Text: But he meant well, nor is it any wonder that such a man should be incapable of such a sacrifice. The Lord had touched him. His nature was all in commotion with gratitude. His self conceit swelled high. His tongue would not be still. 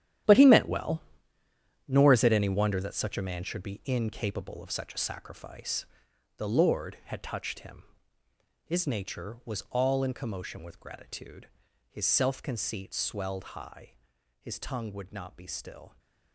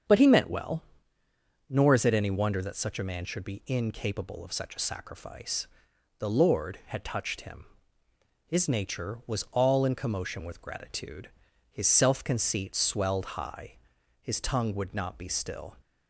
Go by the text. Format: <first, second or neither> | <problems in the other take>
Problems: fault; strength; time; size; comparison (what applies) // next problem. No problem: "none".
second | gets quieter; strong; throughout; 12.5 dB // starts louder than the rest; strong; until 2.1 s; 11 dB; strong in the second